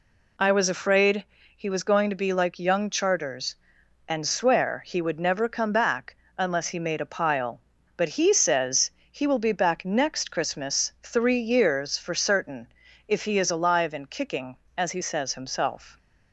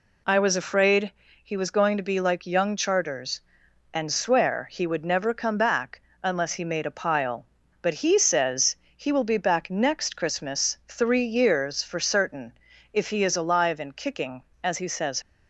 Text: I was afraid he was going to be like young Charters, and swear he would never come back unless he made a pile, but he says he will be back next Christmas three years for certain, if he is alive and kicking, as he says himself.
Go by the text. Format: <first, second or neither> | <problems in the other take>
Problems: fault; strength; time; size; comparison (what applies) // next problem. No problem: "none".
first | pauses between "afraid" and "he"; slight; at 1.1 s; 0.32 s long; slight in the first // pauses between "back" and "unless"; slight; at 5.9 s; 0.22 s long; slight in the first // pauses between "says" and "he"; slight; at 8.7 s; 0.20 s long; slight in the first // stops before "himself"; at 15.2 s